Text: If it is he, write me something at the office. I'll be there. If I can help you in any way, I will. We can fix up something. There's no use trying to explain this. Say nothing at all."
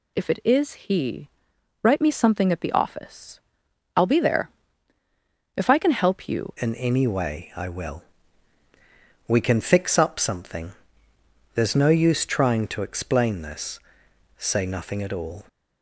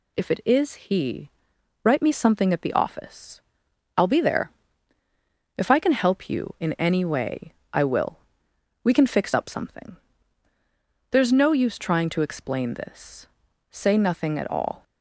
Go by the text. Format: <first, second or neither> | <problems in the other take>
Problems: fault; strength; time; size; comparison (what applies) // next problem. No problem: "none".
second | changes voice at "in"; from 6.5 s on; 8.9 s long